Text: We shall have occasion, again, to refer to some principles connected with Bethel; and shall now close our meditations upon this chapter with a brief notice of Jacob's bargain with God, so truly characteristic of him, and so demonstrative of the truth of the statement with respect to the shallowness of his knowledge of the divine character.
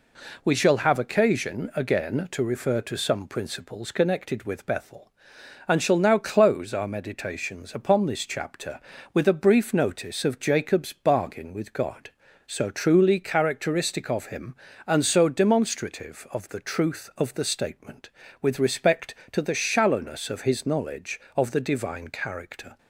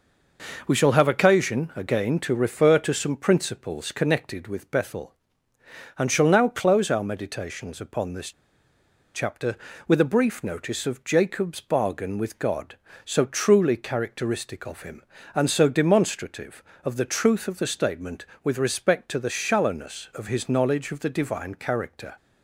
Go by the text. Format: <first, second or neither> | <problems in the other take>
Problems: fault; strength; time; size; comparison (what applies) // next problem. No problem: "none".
first | pauses between "this" and "chapter"; noticeable; at 8.3 s; 0.83 s long